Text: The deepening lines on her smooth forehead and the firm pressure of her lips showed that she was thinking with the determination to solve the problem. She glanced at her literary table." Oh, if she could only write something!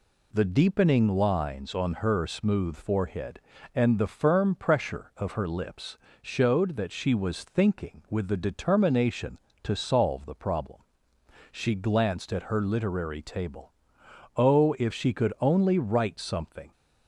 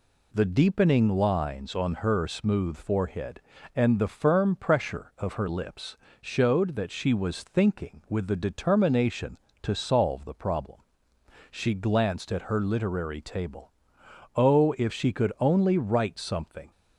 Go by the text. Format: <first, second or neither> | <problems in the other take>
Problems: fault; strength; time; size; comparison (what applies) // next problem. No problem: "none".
neither | pauses between "lips" and "showed"; slight; the same in both